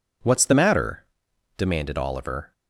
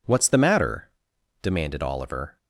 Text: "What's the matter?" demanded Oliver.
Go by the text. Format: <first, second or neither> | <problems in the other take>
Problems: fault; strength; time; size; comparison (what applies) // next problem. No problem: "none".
neither | none